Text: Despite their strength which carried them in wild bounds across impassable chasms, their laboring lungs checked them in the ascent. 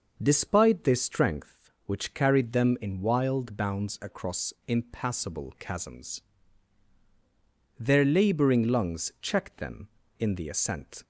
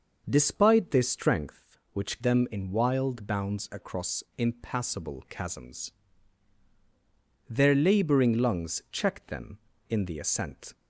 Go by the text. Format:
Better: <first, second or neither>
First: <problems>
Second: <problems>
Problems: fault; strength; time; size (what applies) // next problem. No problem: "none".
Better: first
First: none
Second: skips "carried"; at 2.2 s